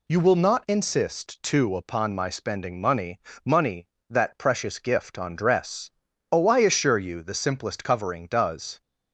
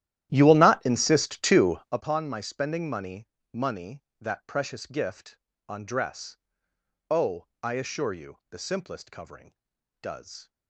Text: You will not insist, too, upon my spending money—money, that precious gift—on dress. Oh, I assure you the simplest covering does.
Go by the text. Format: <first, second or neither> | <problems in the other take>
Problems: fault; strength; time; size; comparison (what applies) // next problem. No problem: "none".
first | starts louder than the rest; strong; until 2.1 s; 12.5 dB